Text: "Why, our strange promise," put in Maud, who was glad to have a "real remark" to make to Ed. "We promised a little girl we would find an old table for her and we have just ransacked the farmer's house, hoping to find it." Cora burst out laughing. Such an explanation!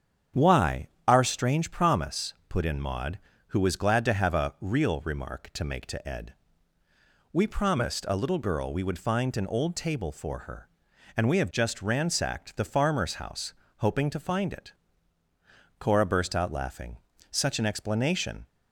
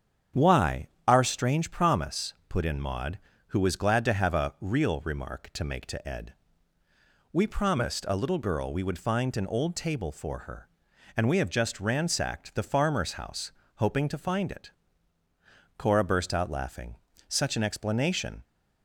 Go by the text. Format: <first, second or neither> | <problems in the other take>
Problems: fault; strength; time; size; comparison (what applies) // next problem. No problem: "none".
neither | starts louder than the rest; strong; the same in both